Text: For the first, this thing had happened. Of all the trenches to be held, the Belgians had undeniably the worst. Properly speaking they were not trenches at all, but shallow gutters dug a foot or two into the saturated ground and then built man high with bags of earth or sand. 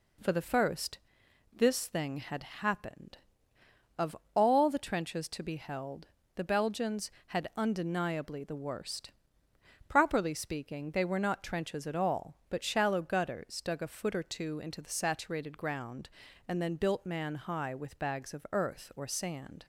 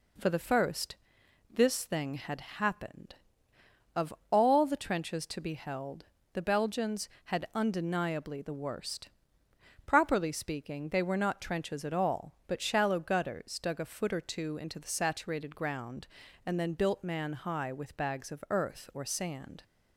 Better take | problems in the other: neither | pauses between "Of" and "all"; slight; the same in both

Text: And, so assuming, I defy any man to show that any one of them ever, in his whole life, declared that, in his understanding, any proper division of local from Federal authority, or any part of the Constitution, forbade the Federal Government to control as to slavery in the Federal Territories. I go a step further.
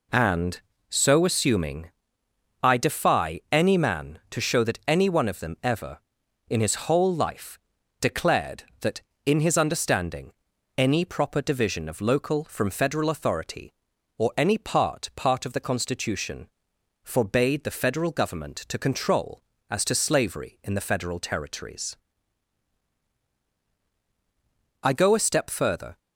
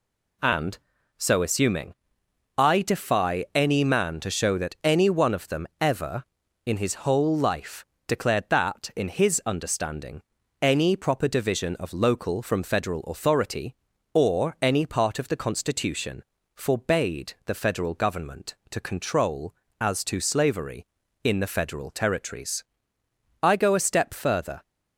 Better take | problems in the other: second | says "part" twice; at 15.1 s

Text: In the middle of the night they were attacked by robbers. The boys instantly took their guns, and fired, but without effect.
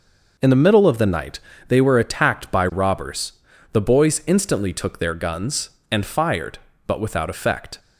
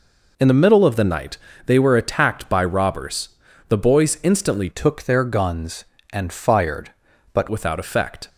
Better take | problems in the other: first | pauses between "night" and "they"; slight; at 1.3 s; 0.28 s long; slight in the first // changes voice from "took" to "but"; from 4.6 to 7.4 s; 2.8 s long

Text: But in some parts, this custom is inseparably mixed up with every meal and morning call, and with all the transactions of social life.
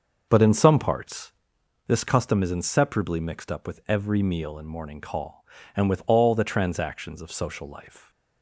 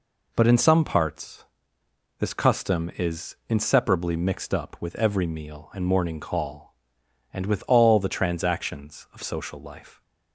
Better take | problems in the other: second | starts louder than the rest; noticeable; until 1.5 s; 6 dB

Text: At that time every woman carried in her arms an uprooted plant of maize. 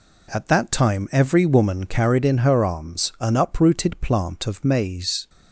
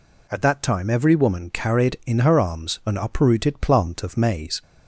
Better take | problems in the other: neither | none

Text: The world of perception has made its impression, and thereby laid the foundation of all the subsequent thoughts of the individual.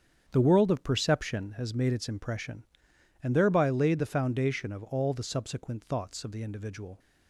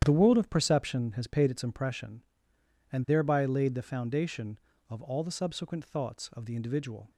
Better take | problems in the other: first | starts louder than the rest; strong; until 1.0 s; 10 dB; strong in the first // says "paid" for "made"; at 1.2 s

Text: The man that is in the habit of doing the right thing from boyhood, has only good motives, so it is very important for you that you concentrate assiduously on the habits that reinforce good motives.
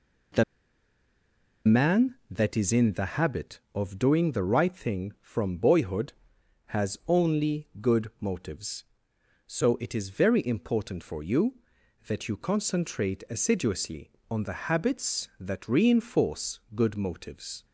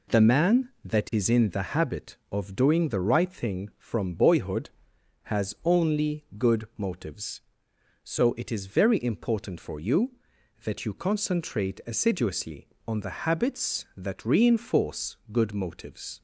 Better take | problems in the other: second | pauses between "The" and "man"; at 0.4 s; 1.2 s long // pauses between "reinforce" and "good"; slight; at 16.5 s; 0.16 s long; slight in the second

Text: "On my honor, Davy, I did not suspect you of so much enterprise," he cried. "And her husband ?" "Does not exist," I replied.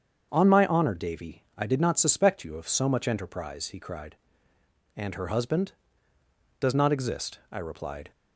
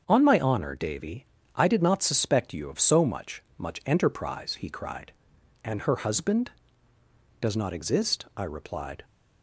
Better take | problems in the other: first | starts louder than the rest; strong; until 1.0 s; 7.5 dB; strong in the first // says "much" twice; at 3.5 s

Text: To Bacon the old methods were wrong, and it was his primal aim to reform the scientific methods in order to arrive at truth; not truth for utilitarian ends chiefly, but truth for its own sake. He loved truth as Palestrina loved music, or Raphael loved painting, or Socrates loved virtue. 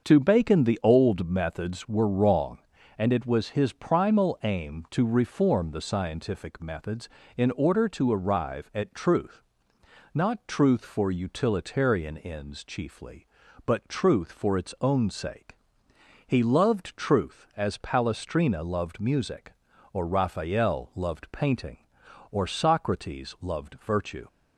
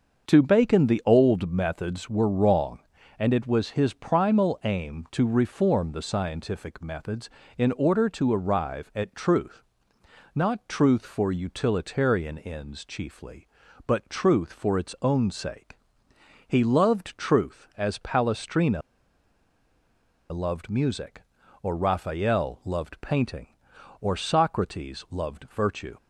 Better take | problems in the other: first | starts louder than the rest; until 1.3 s; 6.5 dB; also in the first // pauses between "Palestrina" and "loved"; strong; at 18.8 s; 1.4 s long

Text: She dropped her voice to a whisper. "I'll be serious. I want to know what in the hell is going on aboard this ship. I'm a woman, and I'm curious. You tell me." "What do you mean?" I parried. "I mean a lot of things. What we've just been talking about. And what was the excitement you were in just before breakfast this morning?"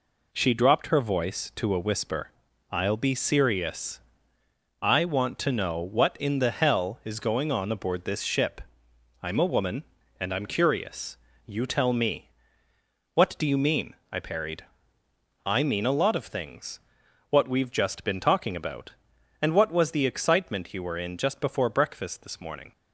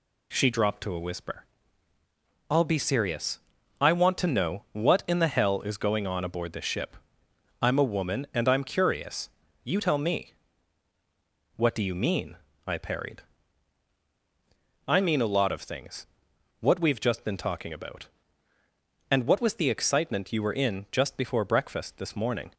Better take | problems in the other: first | skips "her voice"; at 0.8 s

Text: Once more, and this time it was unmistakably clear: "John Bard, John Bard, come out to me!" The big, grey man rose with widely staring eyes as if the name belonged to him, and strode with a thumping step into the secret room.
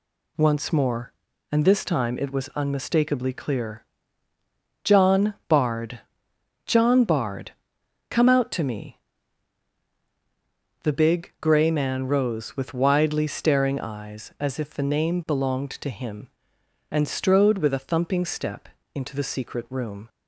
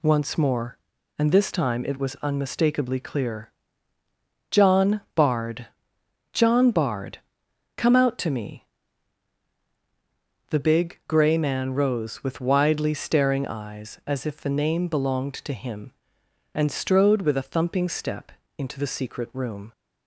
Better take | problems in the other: neither | pauses between "step" and "into"; slight; the same in both

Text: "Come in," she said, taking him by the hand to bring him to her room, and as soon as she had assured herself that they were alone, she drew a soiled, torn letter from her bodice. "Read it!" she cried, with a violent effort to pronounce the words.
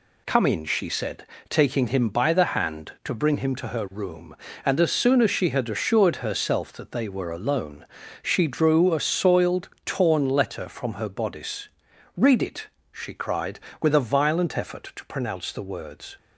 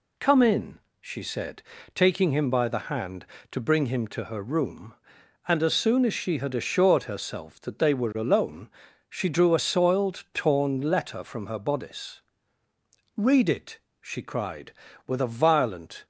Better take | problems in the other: first | stops before "effort to pronounce the words"; at 16.0 s

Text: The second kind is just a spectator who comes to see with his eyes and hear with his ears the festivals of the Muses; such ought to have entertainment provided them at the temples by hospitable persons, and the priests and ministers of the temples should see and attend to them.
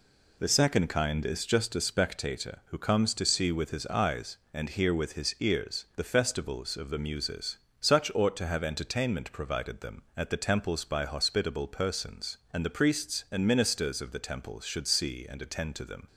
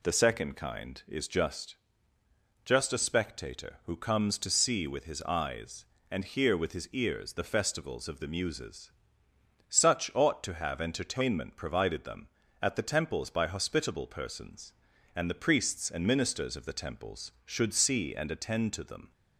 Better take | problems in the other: first | says "just" twice; at 2.6 s

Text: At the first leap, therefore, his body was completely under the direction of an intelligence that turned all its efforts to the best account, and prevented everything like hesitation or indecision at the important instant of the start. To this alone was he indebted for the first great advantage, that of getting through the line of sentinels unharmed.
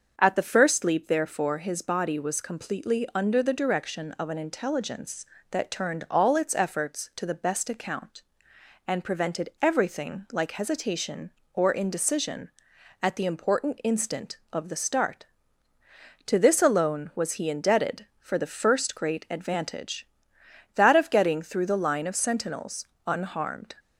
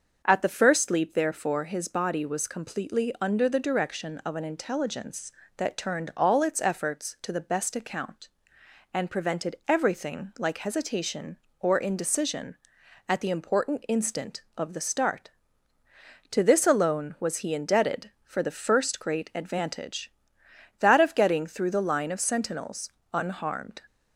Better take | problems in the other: neither | starts louder than the rest; the same in both // pauses between "sentinels" and "unharmed"; slight; the same in both

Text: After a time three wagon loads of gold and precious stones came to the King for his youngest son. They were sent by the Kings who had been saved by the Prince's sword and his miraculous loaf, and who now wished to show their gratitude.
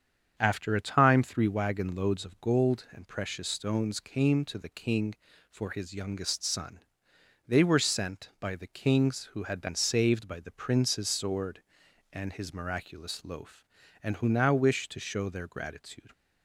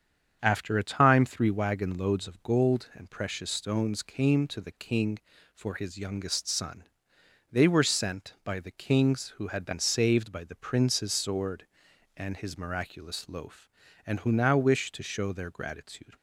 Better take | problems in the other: neither | starts louder than the rest; strong; the same in both

